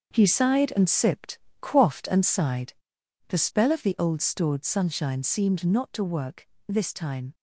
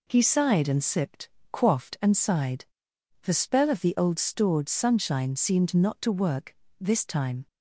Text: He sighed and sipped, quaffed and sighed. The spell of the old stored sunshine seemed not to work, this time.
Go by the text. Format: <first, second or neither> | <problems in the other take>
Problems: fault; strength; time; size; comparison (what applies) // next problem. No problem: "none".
second | gets quieter; strong; throughout; 9.5 dB